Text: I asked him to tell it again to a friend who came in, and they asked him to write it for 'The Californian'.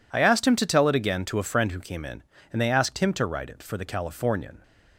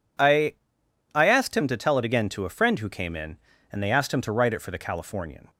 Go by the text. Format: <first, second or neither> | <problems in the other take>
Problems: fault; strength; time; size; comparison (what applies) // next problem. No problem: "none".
first | says "I" twice; at 1.1 s